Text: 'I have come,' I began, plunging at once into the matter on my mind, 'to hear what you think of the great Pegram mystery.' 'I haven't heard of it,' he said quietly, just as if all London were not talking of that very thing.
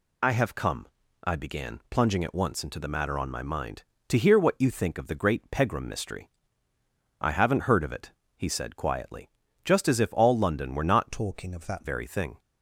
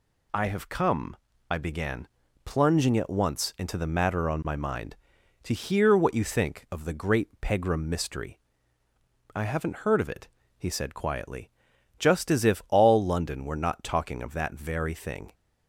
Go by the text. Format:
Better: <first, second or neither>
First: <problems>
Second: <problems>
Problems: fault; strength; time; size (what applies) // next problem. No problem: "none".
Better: second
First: changes voice from "talking" to "that"; from 11.1 to 11.8 s; 0.7 s long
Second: none